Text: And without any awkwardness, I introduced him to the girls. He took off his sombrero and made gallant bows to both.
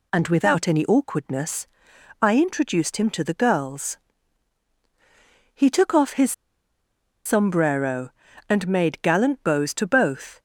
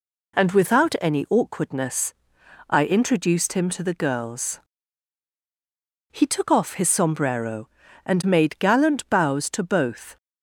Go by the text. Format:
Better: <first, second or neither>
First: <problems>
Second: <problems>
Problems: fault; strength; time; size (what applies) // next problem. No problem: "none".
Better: second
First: pauses between "his" and "sombrero"; noticeable; at 6.3 s; 0.93 s long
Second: none